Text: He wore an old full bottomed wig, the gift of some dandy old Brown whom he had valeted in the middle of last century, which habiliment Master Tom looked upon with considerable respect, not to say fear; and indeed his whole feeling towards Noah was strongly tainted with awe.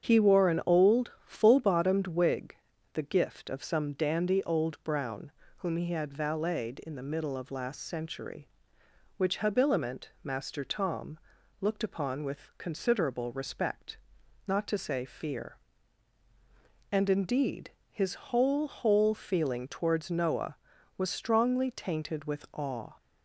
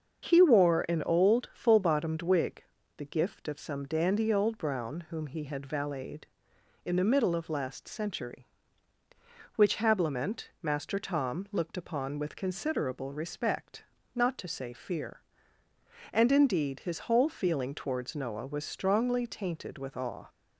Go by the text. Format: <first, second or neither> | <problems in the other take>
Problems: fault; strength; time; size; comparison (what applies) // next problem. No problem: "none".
second | starts louder than the rest; strong; until 1.0 s; 8.5 dB; also in the second // pauses between "Brown" and "whom"; slight; at 5.3 s; 0.24 s long // pauses between "Tom" and "looked"; at 11.1 s; 0.44 s long // pauses between "indeed" and "his"; slight; at 17.7 s; 0.20 s long // says "whole" twice; at 18.6 s